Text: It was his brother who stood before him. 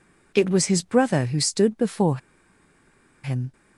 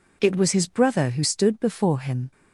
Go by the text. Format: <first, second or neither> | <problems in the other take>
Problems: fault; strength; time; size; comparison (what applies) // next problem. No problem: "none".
second | pauses between "before" and "him"; at 2.1 s; 1.0 s long